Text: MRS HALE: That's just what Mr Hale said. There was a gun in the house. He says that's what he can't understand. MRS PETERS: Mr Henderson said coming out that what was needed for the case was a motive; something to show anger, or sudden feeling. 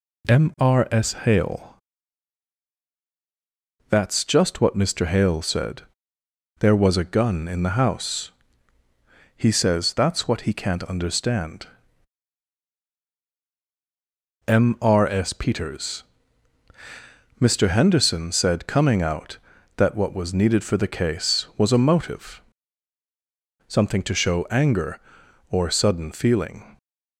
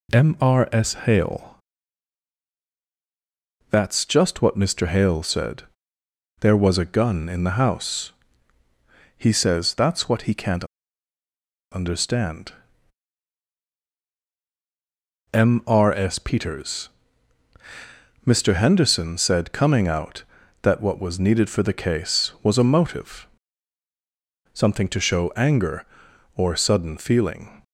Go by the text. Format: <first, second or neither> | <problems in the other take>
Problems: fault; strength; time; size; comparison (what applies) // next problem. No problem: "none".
first | pauses between "can't" and "understand"; at 10.6 s; 1.0 s long